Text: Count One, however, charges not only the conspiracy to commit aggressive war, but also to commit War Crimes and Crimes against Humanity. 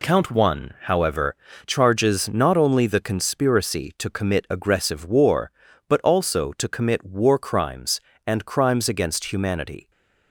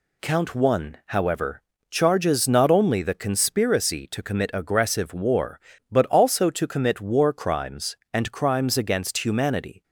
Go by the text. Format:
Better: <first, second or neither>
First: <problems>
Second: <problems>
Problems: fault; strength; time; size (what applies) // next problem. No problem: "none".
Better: neither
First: none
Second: none